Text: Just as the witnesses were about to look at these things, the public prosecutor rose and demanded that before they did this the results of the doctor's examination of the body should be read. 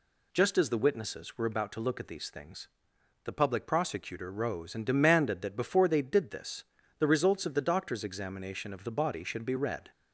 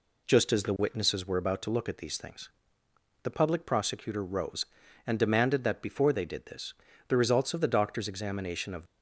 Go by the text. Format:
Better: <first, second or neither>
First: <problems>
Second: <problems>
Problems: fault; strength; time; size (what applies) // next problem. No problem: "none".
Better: first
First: pauses between "this" and "the"; slight; at 6.6 s; 0.34 s long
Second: pauses between "this" and "the"; slight; at 6.7 s; 0.34 s long // stops before "the body should be read"; at 8.8 s